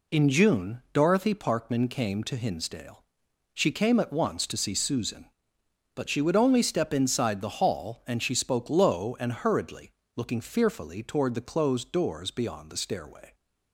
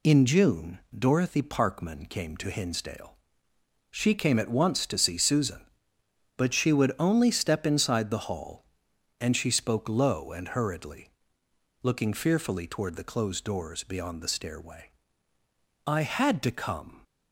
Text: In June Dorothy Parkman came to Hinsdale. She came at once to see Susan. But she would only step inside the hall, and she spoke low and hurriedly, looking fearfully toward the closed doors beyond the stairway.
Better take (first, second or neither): first